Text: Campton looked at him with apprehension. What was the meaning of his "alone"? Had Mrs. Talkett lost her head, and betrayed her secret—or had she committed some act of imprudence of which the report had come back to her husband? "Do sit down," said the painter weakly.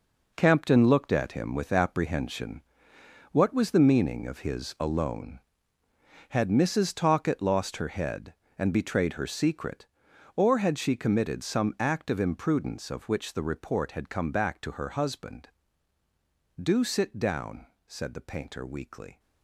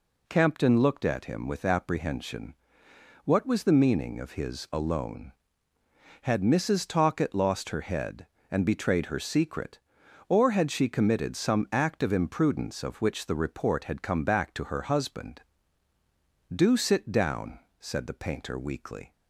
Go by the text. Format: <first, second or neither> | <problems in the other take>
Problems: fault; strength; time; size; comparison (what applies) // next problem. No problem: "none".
second | gets quieter; strong; throughout; 10 dB